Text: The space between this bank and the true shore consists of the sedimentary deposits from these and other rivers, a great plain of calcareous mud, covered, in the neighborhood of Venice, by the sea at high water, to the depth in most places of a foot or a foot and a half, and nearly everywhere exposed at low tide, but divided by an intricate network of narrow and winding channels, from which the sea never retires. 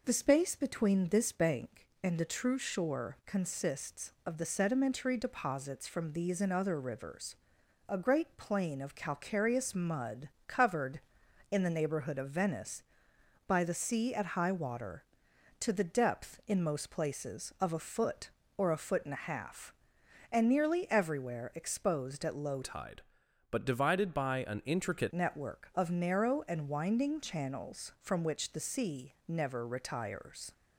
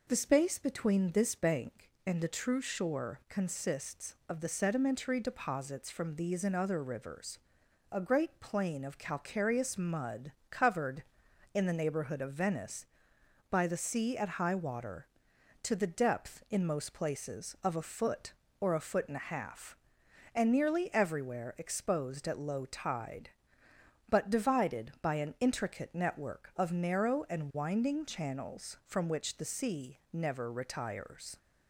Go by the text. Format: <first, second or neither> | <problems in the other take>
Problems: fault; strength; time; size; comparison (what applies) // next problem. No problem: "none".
second | changes voice from "tide" to "intricate"; from 22.6 to 25.1 s; 2.5 s long